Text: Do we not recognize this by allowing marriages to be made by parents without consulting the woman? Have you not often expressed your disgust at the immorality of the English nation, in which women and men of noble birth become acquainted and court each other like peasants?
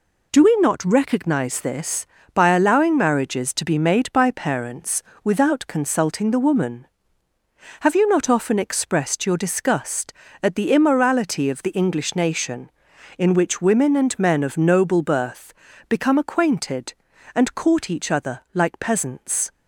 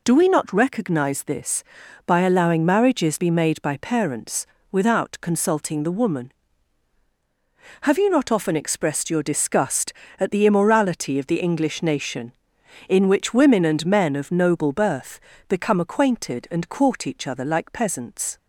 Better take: first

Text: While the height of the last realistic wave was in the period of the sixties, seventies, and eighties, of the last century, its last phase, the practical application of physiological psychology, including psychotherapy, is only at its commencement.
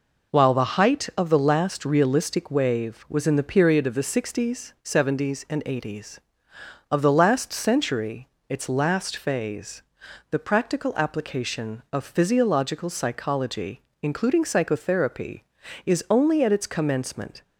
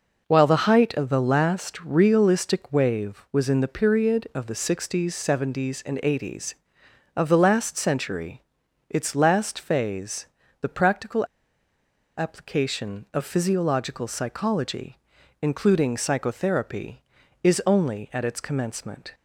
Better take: first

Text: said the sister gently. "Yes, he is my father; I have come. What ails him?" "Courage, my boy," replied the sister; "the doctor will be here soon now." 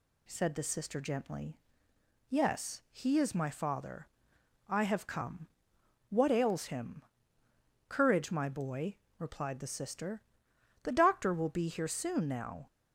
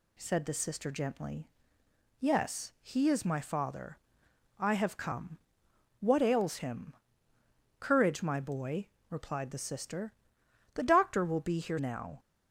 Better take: first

